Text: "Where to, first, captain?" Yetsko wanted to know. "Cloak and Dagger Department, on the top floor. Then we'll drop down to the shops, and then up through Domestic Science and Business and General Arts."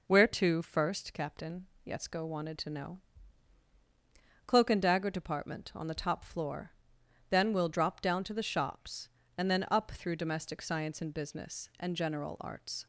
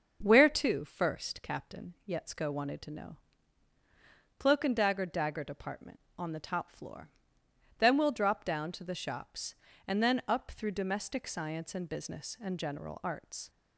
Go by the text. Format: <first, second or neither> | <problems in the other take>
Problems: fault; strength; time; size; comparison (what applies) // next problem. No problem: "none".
first | starts louder than the rest; until 1.2 s; 6.5 dB // says "Dagger" twice; at 5.0 s